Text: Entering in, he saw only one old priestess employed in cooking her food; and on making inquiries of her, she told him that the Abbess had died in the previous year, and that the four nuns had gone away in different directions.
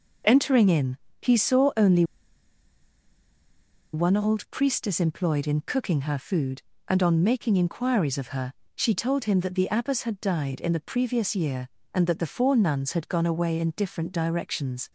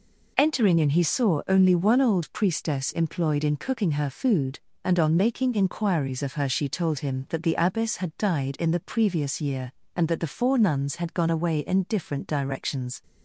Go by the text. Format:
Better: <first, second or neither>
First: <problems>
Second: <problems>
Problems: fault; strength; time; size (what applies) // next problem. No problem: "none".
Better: second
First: pauses between "only" and "one"; strong; at 2.0 s; 1.8 s long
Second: none